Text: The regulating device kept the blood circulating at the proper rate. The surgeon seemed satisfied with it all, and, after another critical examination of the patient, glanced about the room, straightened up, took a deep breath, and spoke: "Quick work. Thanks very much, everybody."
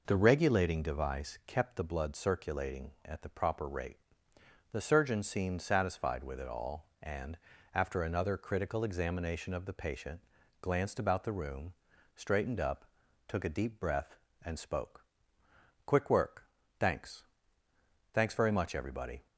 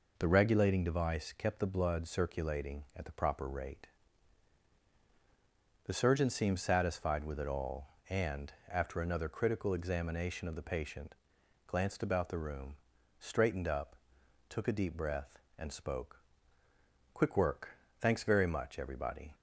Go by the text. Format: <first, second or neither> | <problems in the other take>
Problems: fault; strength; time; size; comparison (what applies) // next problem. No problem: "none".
second | says "Thanks" twice; at 18.1 s